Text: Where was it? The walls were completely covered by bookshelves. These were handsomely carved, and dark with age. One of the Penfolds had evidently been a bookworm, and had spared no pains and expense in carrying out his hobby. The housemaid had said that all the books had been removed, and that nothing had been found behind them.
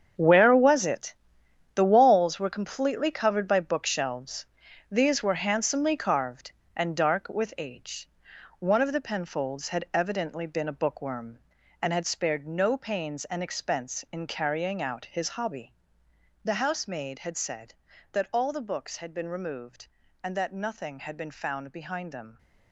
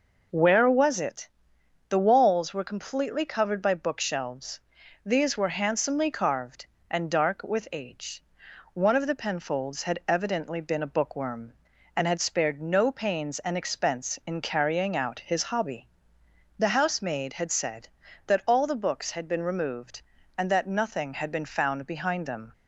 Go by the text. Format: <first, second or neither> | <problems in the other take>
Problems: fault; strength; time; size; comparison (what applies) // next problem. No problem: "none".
second | gets quieter; strong; throughout; 12 dB